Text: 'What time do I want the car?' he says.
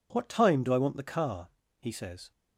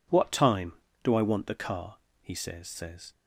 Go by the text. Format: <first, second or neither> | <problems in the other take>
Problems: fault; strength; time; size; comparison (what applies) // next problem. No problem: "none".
first | says "says" twice; at 2.6 s